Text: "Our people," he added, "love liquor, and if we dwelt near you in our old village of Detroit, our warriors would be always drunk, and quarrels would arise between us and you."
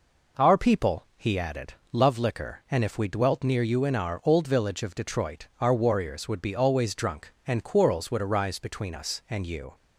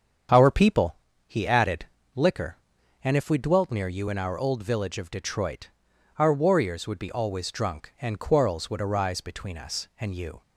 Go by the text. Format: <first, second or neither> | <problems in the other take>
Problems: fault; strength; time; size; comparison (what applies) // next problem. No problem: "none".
first | starts louder than the rest; strong; until 1.6 s; 7.5 dB // skips "love"; at 2.0 s